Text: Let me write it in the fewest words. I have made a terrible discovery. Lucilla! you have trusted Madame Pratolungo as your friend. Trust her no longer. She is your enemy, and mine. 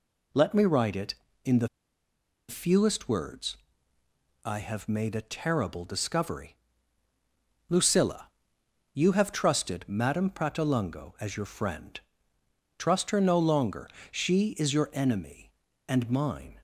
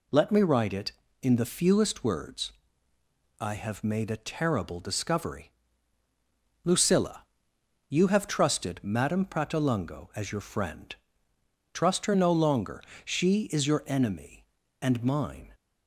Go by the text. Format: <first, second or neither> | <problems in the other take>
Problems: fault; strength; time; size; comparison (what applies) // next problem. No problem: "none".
second | pauses between "the" and "fewest"; noticeable; at 1.6 s; 0.81 s long